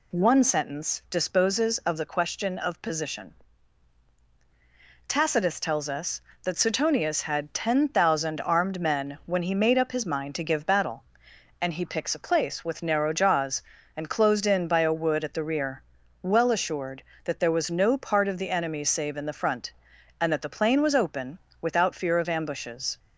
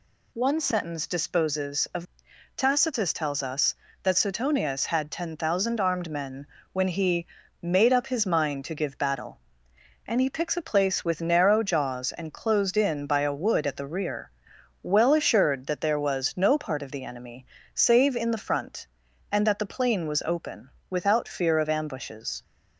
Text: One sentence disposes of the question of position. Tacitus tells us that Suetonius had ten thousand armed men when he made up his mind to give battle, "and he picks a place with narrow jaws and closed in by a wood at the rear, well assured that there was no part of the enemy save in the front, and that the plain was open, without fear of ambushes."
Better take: first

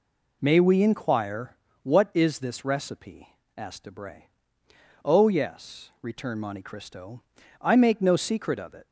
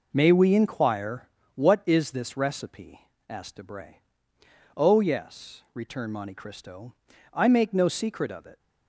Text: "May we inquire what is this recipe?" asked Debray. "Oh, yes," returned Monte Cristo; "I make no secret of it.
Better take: first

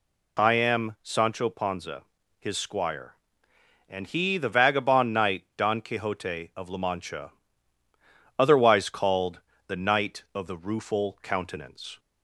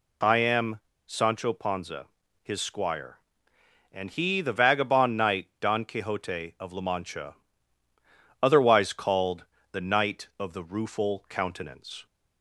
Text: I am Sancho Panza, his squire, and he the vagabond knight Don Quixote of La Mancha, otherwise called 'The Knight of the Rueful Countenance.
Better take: first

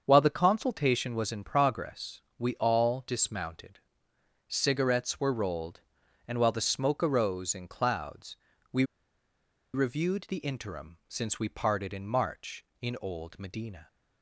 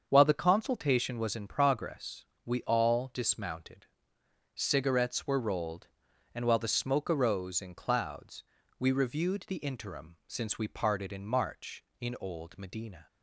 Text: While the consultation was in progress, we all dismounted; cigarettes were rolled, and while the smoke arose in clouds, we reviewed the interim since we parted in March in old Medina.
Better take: second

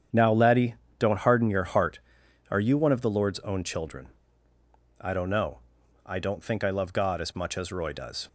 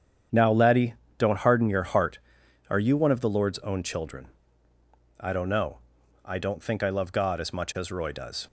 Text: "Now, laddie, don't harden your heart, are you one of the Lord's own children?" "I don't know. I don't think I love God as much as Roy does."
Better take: neither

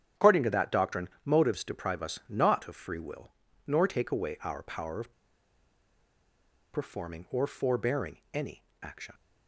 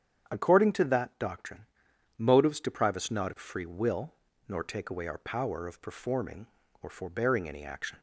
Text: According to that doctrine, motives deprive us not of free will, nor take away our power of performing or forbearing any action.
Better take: second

